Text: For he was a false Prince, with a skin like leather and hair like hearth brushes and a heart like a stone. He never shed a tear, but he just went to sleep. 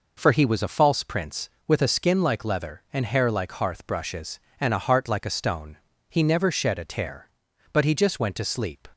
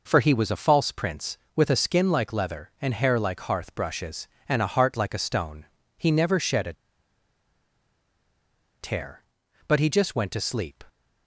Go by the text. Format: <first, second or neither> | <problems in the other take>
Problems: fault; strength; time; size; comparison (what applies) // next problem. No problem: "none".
first | pauses between "a" and "tear"; strong; at 6.7 s; 2.0 s long